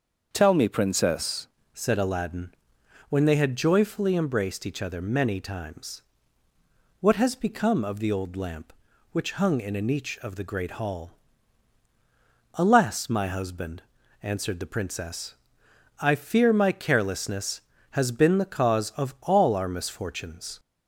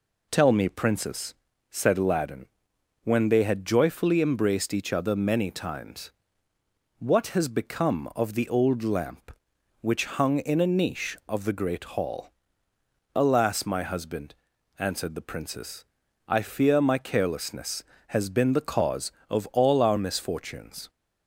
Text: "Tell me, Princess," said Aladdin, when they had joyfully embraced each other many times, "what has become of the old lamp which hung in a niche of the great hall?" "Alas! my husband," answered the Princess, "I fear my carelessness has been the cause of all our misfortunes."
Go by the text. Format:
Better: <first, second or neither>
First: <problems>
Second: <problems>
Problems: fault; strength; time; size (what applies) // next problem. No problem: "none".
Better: second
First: starts louder than the rest; until 1.3 s; 6.5 dB // changes voice at "said"; from 1.7 s on; 18.8 s long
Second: none